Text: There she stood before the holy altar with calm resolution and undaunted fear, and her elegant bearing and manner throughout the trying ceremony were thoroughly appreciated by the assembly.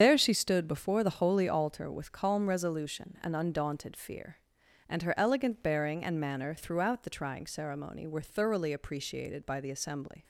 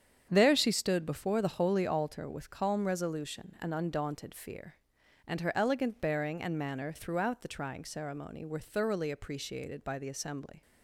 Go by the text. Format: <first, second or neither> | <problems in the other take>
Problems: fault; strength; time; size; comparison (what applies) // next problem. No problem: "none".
second | loses the start of "There"; at 0.0 s; 80 ms // starts louder than the rest; strong; until 1.0 s; 7.5 dB; strong in the second